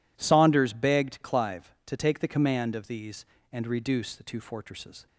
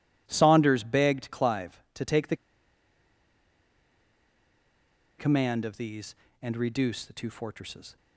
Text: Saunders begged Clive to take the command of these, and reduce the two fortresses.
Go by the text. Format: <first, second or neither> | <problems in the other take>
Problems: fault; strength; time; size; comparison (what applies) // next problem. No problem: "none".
first | pauses between "the" and "command"; strong; at 2.3 s; 2.8 s long